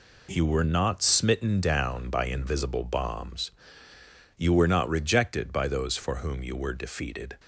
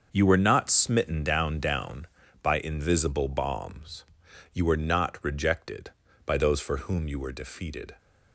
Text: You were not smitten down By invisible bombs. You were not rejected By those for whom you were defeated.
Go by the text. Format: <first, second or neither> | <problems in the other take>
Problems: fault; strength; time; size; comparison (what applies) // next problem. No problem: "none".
first | starts louder than the rest; until 1.1 s; 6 dB // says "down" twice; at 1.5 s